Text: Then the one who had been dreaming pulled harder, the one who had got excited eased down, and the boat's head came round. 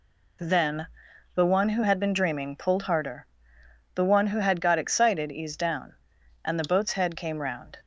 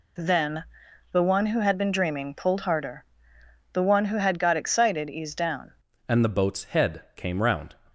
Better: first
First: pauses between "Then" and "the"; noticeable; at 0.8 s; 0.48 s long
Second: pauses between "Then" and "the"; noticeable; at 0.6 s; 0.48 s long // changes voice at "and"; from 6.0 s on; 1.7 s long

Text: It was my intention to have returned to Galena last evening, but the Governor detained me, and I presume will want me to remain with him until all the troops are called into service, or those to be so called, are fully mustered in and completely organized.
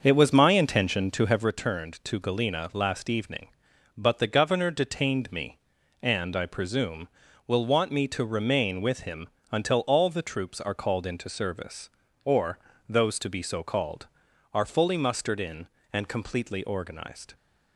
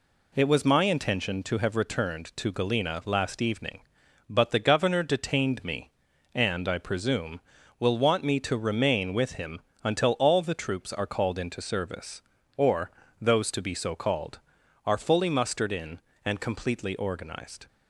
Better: second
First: starts louder than the rest; until 1.5 s; 6.5 dB // pauses between "him" and "until"; slight; at 9.2 s; 0.26 s long // pauses between "or" and "those"; slight; at 12.5 s; 0.30 s long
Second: pauses between "him" and "until"; slight; at 9.5 s; 0.26 s long // pauses between "or" and "those"; slight; at 12.9 s; 0.30 s long

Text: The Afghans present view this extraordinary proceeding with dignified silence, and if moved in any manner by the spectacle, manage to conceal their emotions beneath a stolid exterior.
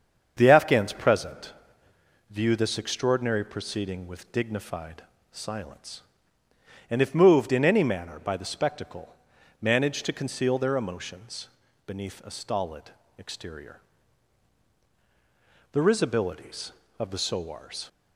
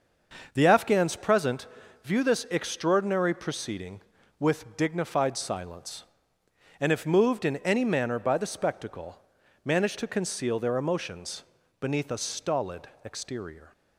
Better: second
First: starts louder than the rest; strong; until 1.3 s; 7 dB // pauses between "present" and "view"; noticeable; at 1.5 s; 0.78 s long // pauses between "dignified" and "silence"; slight; at 5.0 s; 0.30 s long // pauses between "emotions" and "beneath"; at 11.4 s; 0.40 s long // pauses between "stolid" and "exterior"; slight; at 12.9 s; 0.26 s long // goes on to say "The risibilities of the sowars"; strong; from 15.7 s on; 2.1 s long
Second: starts louder than the rest; until 1.5 s; 6.5 dB // pauses between "present" and "view"; at 1.6 s; 0.38 s long // pauses between "emotions" and "beneath"; slight; at 11.4 s; 0.36 s long // pauses between "stolid" and "exterior"; slight; at 12.8 s; 0.16 s long

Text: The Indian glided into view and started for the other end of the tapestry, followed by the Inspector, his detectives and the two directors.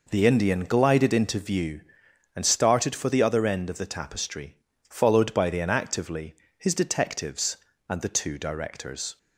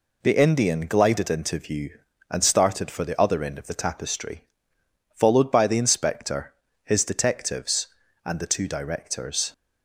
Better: second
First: says "Inactively" for "Inspector"; at 5.5 s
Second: none

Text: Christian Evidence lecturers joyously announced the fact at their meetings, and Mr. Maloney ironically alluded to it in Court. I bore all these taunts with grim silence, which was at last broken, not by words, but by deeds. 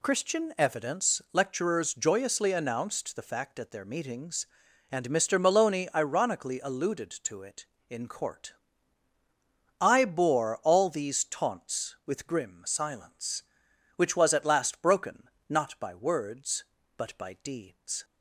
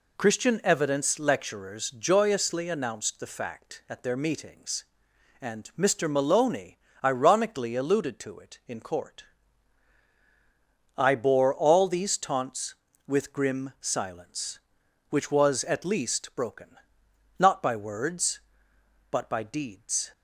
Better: first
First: none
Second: pauses between "Maloney" and "ironically"; slight; at 6.7 s; 0.26 s long // says "least" for "last"; at 15.8 s

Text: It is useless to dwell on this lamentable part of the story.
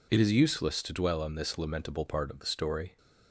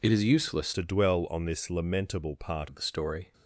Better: first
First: none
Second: changes voice from "to" to "part"; from 0.7 to 2.6 s; 1.9 s long

